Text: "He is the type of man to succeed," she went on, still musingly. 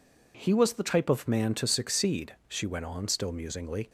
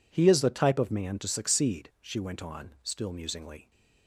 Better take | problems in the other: second | says "was" for "is"; at 0.5 s

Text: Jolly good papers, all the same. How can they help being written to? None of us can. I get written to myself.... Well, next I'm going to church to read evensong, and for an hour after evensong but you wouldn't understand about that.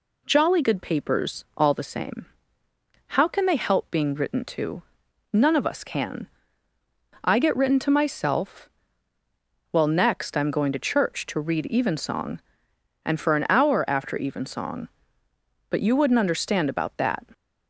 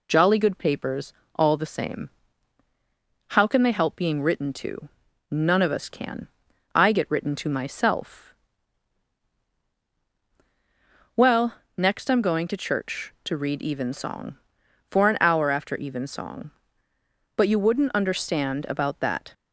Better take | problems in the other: first | skips "and"; at 14.6 s

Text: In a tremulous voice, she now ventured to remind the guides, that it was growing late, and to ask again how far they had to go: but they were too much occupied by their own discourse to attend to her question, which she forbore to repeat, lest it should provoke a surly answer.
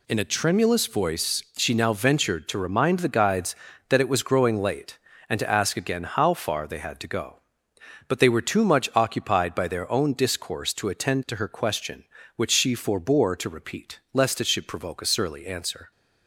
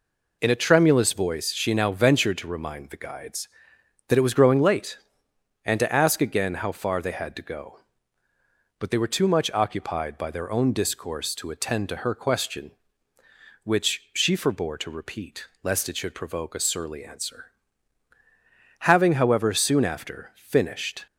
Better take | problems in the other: first | goes on to say "Having however soon after finished"; strong; from 18.8 s on; 2.2 s long

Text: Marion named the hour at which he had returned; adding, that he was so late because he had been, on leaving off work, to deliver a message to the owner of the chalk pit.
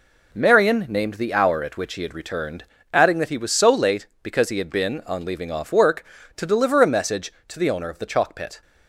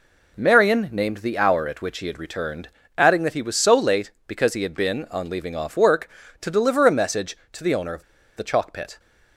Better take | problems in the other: first | pauses between "of" and "the"; slight; at 8.0 s; 0.34 s long

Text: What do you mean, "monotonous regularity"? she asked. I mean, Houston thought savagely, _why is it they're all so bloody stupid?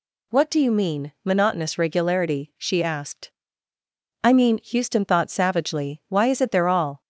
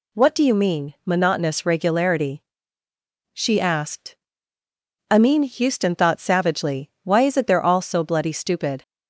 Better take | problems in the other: second | stops before "so bloody stupid"; at 7.0 s

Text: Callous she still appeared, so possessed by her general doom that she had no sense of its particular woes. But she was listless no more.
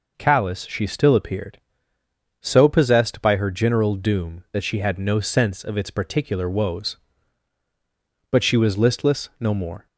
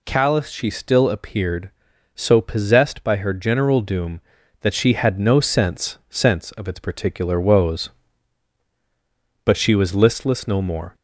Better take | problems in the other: first | says "sense" twice; at 6.0 s

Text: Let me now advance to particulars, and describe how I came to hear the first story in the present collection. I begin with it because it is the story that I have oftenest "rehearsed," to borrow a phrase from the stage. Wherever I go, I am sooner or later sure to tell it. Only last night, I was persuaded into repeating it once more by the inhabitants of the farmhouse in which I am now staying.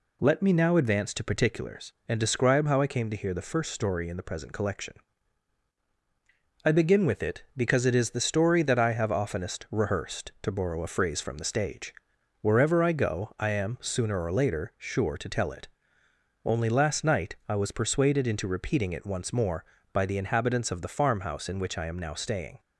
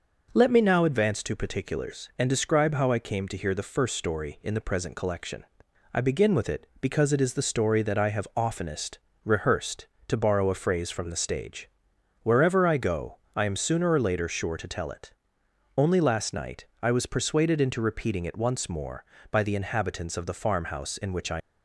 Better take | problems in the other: first | pauses between "oftenest" and "rehearsed"; slight; at 8.9 s; 0.26 s long // stops before "am now staying"; at 21.4 s

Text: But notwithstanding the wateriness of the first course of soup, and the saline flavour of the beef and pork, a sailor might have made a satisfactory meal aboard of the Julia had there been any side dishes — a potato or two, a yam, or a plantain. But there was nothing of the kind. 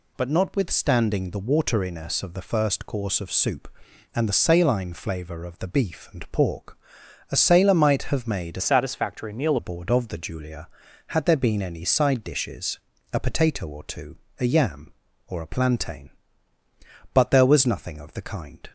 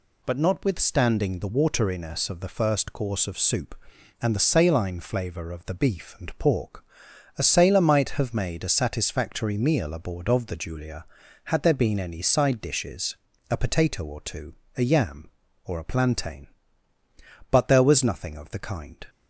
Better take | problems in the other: second | changes voice from "satisfactory" to "meal"; from 8.6 to 9.5 s; 0.9 s long

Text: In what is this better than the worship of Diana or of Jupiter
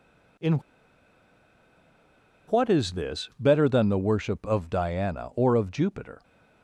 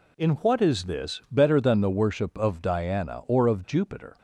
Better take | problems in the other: second | pauses between "In" and "what"; strong; at 0.5 s; 1.9 s long

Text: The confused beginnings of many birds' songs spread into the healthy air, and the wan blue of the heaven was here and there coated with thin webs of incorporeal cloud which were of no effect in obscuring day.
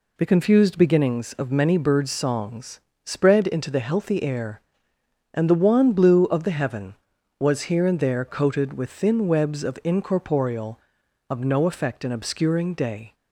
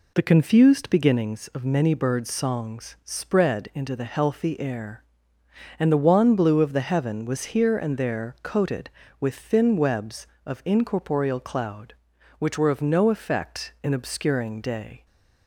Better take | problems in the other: second | pauses between "songs" and "spread"; slight; at 2.8 s; 0.22 s long // skips "cloud which were"; at 11.0 s

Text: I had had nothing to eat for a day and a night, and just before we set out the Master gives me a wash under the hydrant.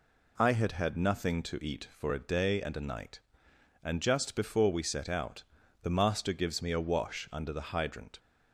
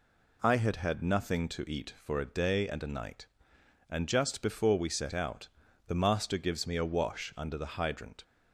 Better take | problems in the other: neither | pauses between "out" and "the"; the same in both

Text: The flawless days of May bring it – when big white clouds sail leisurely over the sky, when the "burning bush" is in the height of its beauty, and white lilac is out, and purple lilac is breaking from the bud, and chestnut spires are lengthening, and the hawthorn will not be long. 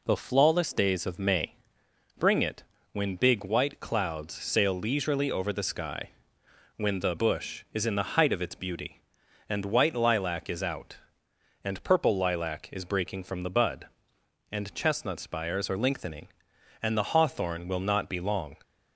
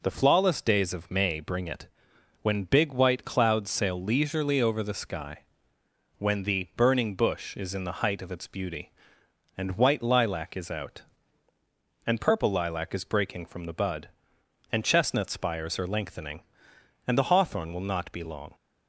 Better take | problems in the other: second | pauses between "May" and "bring"; noticeable; at 1.5 s; 0.64 s long // skips "burning"; at 7.1 s

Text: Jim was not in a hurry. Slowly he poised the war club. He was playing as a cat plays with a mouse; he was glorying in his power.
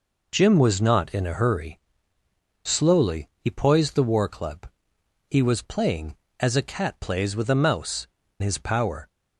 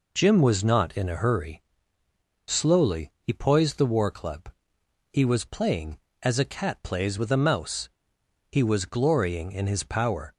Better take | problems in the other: second | skips "he was glorying in"; at 8.2 s

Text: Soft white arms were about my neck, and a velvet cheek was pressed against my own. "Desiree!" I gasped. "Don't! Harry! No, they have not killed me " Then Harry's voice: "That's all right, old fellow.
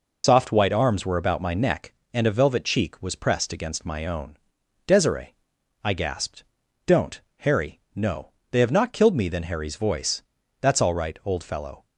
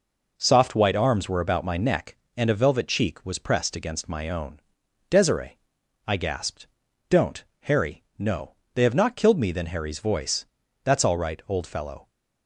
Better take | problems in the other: second | loses the start of "Soft"; at 0.2 s; 105 ms

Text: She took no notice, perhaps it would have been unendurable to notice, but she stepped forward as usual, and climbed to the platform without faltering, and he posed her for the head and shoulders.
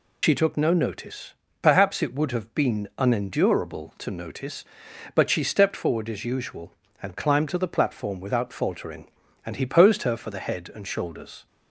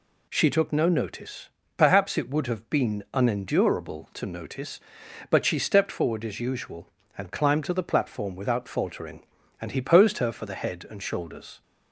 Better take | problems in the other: second | loses the start of "She"; at 0.2 s; 85 ms

